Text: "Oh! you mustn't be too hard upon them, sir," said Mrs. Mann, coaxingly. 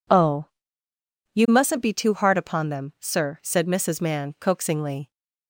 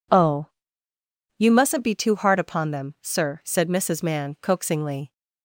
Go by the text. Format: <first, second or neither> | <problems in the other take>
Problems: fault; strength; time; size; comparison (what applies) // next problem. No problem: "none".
neither | none